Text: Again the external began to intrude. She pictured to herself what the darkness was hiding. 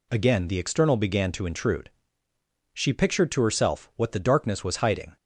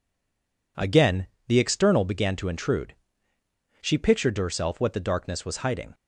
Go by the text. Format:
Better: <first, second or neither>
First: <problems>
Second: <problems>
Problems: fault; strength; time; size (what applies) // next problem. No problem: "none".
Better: first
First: none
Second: stays silent before the first word; slight; until 0.7 s; 0.7 s long // pauses between "Again" and "the"; slight; at 1.2 s; 0.22 s long